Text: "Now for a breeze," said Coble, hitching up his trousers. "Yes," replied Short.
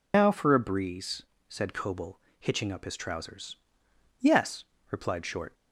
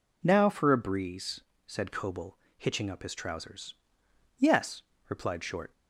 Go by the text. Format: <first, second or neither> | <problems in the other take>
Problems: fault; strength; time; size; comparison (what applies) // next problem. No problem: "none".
second | loses the start of "Now"; at 0.1 s; 90 ms